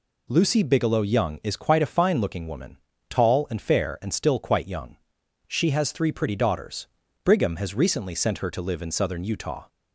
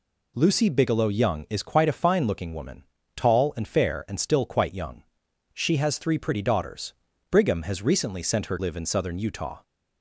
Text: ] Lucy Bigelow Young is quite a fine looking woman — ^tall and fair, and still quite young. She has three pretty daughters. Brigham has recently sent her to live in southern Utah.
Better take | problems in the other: first | skips "to"; at 8.5 s

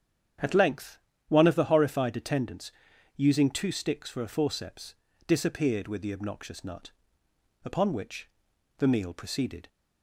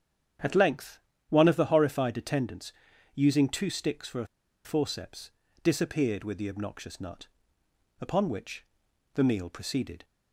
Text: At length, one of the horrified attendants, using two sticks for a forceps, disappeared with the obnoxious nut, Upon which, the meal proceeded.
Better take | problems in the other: first | starts louder than the rest; strong; until 1.7 s; 8.5 dB; strong in the first // pauses between "a" and "forceps"; at 4.2 s; 0.38 s long

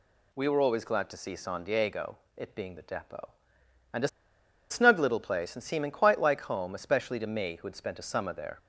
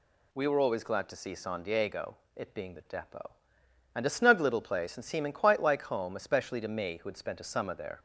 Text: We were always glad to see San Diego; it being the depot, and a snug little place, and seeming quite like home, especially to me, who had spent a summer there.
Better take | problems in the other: second | pauses between "a" and "snug"; noticeable; at 4.0 s; 0.62 s long

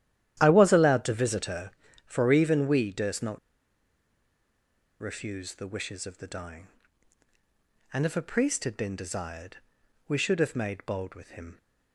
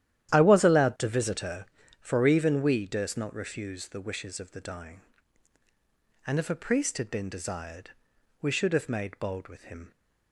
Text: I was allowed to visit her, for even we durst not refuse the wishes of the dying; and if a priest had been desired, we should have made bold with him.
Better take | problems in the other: second | starts louder than the rest; strong; until 1.4 s; 11.5 dB; strong in the second // pauses between "not" and "refuse"; strong; at 3.3 s; 1.6 s long

